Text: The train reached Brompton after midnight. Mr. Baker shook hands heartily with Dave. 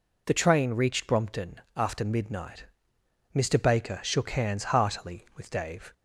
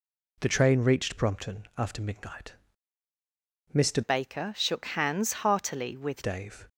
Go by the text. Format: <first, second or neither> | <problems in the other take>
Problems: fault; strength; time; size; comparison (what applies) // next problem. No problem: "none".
first | changes voice from "Baker" to "with"; from 4.0 to 6.2 s; 2.2 s long